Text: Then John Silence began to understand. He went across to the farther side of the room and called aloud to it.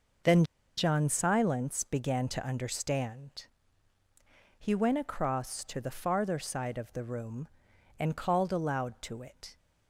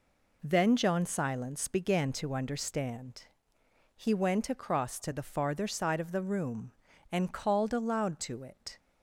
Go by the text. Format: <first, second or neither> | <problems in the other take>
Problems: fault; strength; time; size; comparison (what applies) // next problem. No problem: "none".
second | pauses between "Then" and "John"; slight; at 0.4 s; 0.33 s long